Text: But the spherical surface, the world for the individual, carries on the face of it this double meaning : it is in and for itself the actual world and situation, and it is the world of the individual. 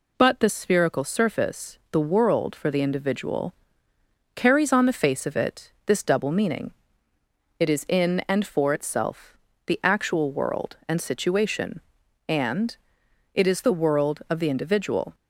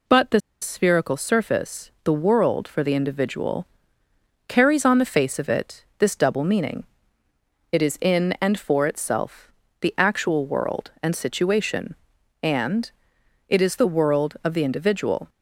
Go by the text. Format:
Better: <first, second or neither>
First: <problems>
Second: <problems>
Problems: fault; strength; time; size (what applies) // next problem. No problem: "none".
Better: first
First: pauses between "itself" and "the"; slight; at 9.3 s; 0.30 s long // pauses between "and" and "it"; noticeable; at 12.7 s; 0.58 s long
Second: pauses between "the" and "spherical"; slight; at 0.3 s; 0.22 s long // pauses between "itself" and "the"; slight; at 9.5 s; 0.30 s long // pauses between "and" and "it"; noticeable; at 12.9 s; 0.58 s long